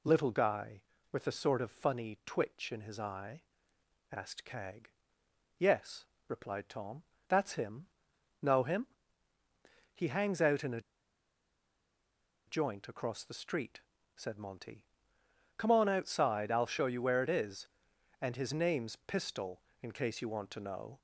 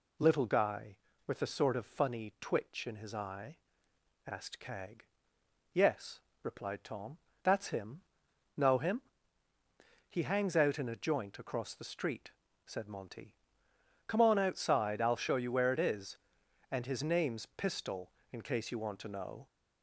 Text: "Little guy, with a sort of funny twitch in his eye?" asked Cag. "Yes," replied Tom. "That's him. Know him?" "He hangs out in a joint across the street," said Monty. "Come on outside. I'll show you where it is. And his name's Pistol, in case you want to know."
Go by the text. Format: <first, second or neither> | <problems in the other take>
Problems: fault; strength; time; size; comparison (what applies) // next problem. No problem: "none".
second | pauses between "a" and "joint"; strong; at 10.7 s; 1.6 s long